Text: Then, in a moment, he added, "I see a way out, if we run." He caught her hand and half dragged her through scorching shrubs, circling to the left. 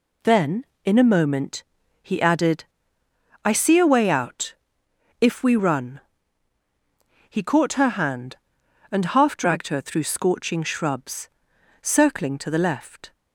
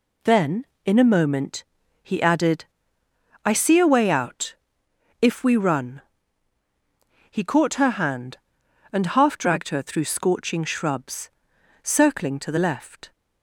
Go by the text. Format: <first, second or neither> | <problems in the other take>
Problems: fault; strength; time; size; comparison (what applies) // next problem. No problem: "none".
neither | none